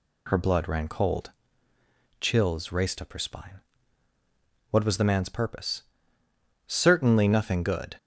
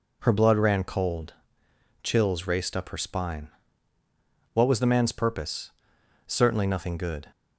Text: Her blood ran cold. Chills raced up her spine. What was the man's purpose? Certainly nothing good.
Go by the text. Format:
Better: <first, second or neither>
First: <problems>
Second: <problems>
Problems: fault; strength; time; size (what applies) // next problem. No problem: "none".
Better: neither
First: none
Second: none